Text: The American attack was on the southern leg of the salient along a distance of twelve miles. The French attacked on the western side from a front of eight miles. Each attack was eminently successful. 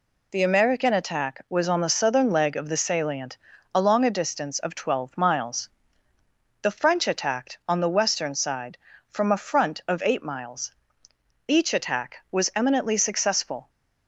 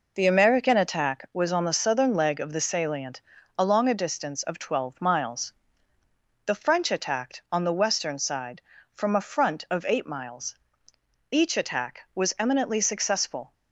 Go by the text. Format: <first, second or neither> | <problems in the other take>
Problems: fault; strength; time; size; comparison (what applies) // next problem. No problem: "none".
first | starts louder than the rest; noticeable; until 1.4 s; 4.5 dB // pauses between "salient" and "along"; slight; at 3.2 s; 0.36 s long; slight in the first